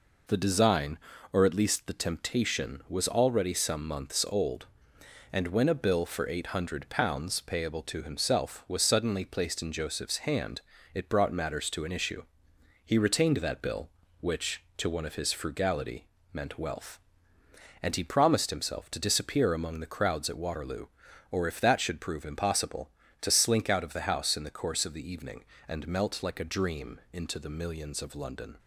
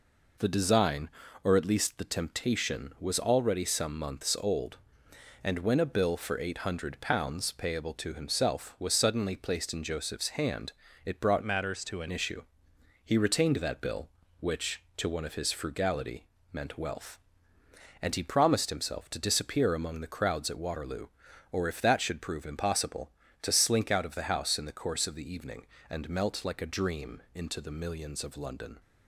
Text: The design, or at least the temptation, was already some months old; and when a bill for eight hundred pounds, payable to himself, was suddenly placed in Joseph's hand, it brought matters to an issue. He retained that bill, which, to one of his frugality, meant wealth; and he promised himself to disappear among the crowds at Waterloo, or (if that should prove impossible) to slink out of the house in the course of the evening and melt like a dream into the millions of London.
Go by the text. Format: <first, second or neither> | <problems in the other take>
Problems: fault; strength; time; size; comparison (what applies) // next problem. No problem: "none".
first | changes voice from "matters" to "an"; from 11.4 to 12.0 s; 0.6 s long